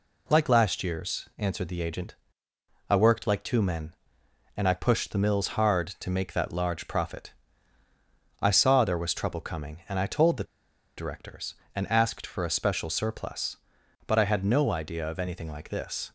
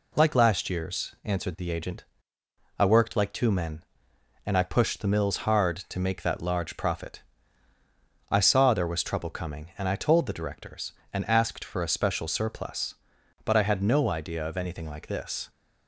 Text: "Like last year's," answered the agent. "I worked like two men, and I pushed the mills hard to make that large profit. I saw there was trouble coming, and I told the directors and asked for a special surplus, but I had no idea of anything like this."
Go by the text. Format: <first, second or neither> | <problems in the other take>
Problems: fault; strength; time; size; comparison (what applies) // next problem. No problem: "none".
second | pauses between "the" and "directors"; noticeable; at 10.4 s; 0.54 s long